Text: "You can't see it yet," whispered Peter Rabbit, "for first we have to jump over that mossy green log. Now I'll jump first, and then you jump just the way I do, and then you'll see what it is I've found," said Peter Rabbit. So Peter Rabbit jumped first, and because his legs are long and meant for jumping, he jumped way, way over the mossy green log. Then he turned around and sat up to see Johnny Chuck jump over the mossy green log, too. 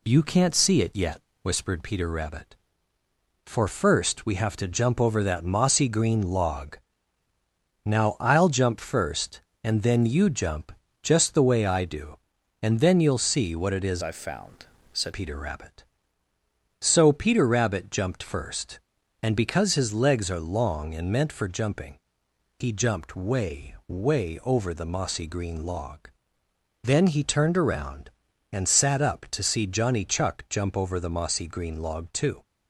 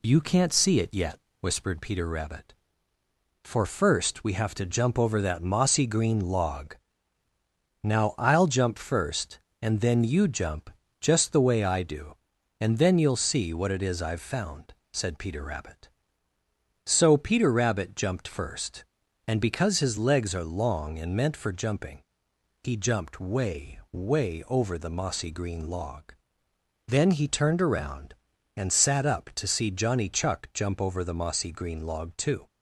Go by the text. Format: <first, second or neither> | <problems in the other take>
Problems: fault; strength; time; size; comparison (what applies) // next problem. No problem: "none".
second | pauses between "jump" and "just"; slight; at 10.7 s; 0.30 s long; slight in the second // changes voice from "I've" to "said"; from 14.0 to 15.1 s; 1.1 s long